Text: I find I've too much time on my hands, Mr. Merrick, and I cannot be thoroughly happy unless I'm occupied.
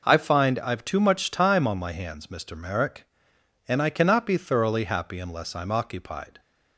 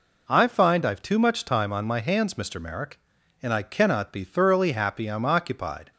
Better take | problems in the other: first | skips "unless"; at 5.0 s

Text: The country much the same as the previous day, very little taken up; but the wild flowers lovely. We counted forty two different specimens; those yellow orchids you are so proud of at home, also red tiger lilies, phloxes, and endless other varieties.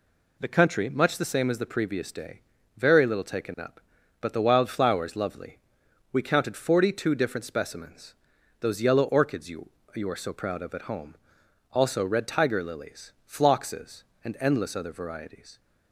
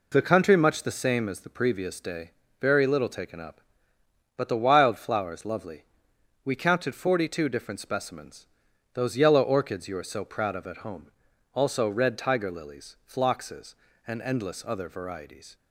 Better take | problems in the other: second | says "you" twice; at 9.9 s

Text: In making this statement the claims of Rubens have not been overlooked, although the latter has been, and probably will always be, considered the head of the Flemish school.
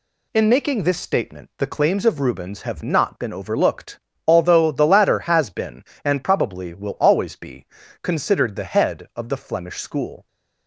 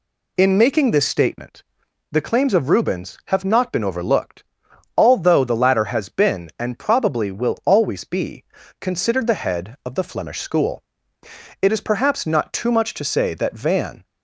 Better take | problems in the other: first | pauses between "statement" and "the"; noticeable; at 1.6 s; 0.48 s long // goes on to say "It is perhaps not too much to say that Van"; strong; from 11.6 s on; 2.4 s long

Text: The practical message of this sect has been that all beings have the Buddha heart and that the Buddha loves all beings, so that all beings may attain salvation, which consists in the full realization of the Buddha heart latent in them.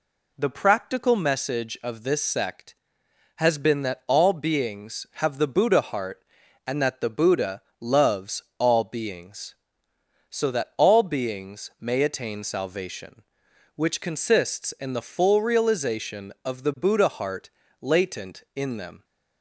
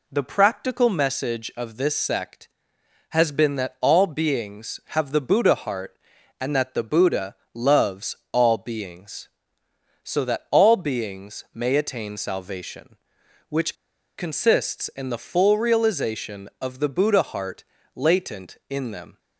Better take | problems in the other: first | pauses between "Buddha" and "loves"; slight; at 7.3 s; 0.18 s long; slight in the first // pauses between "loves" and "all"; slight; at 8.1 s; 0.16 s long; slight in the first // pauses between "which" and "consists"; at 13.7 s; 0.42 s long // pauses between "heart" and "latent"; slight; at 17.6 s; 0.30 s long; slight in the first

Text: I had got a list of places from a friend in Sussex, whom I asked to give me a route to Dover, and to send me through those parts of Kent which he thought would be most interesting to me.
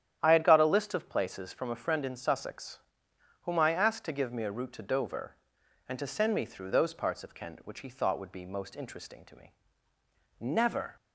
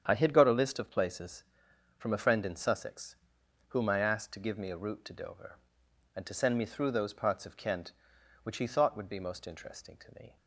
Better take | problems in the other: second | starts louder than the rest; strong; until 1.2 s; 9.5 dB; strong in the second // goes on to say "Never"; from 10.3 s on; 0.56 s long

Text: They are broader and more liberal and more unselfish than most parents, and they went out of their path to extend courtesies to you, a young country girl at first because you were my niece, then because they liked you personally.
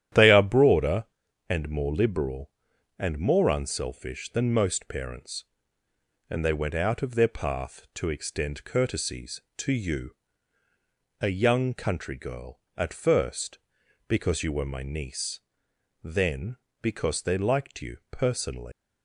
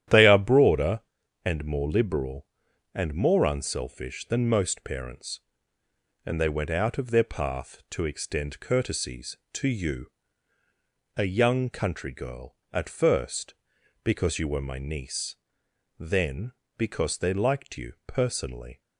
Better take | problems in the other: second | starts louder than the rest; strong; until 1.5 s; 11 dB; strong in the second // leaves "personally" unfinished; at 18.7 s; 135 ms

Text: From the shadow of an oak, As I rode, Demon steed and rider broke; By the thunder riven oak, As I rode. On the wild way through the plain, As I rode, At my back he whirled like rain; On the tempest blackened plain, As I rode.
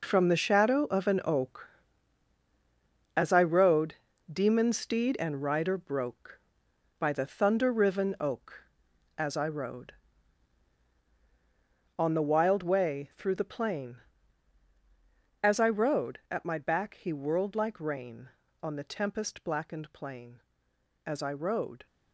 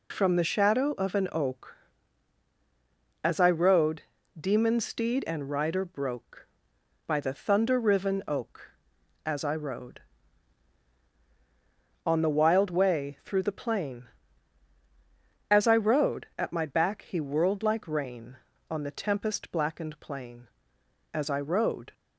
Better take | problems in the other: second | gets quieter; strong; throughout; 11 dB

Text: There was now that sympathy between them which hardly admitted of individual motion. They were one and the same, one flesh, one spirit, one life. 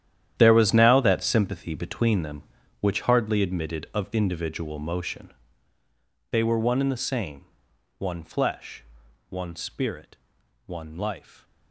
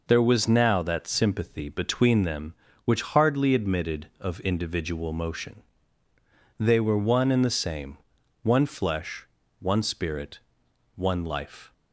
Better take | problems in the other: second | gets quieter; strong; throughout; 14 dB

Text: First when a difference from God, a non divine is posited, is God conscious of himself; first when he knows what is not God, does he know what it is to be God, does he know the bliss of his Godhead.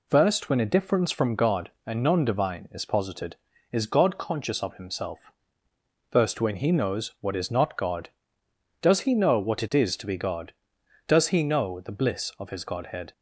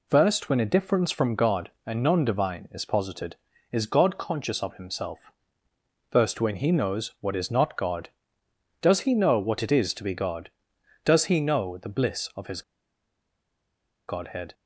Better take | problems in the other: first | pauses between "his" and "Godhead"; strong; at 12.6 s; 1.4 s long

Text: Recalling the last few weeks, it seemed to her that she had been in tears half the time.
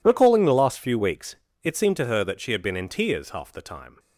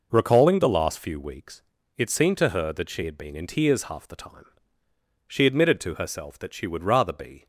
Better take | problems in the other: first | goes on to say "She admitted to herself that she would rather be"; strong; from 5.2 s on; 2.2 s long

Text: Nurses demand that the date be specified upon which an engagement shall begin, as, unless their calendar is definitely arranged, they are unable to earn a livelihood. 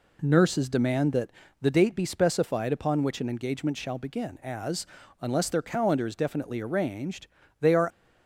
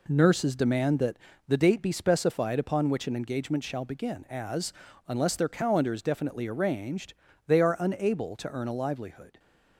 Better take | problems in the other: second | pauses between "that" and "the"; slight; at 1.3 s; 0.30 s long; slight in the second // stops before "unable to earn a livelihood"; at 7.9 s

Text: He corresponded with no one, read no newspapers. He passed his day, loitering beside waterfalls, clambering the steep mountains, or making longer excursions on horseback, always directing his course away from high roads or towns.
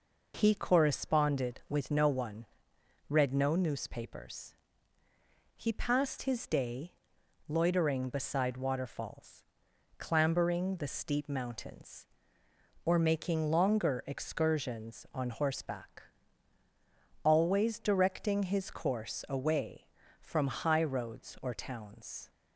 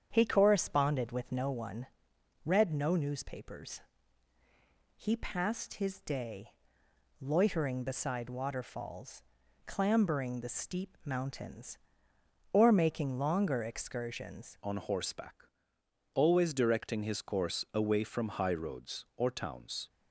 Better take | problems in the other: first | starts louder than the rest; strong; until 1.1 s; 8 dB // changes voice at "on"; from 14.6 s on; 5.2 s long

